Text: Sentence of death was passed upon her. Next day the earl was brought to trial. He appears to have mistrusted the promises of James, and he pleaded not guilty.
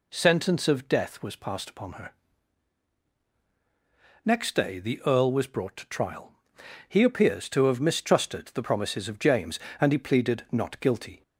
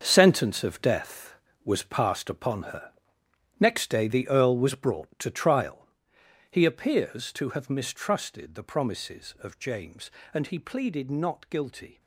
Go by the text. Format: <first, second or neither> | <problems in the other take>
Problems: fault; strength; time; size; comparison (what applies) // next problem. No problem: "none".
first | gets quieter; strong; throughout; 11.5 dB